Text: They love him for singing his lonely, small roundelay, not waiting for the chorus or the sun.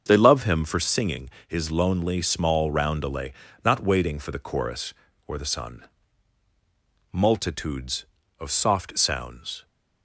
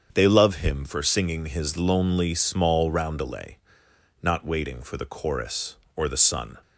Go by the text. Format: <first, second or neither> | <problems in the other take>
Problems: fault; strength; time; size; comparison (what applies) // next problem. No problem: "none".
second | starts louder than the rest; until 1.0 s; 7 dB; strong in the second // pauses between "singing" and "his"; slight; at 1.2 s; 0.18 s long // goes on to say "Multitudes of soft sounds"; strong; from 7.1 s on; 2.5 s long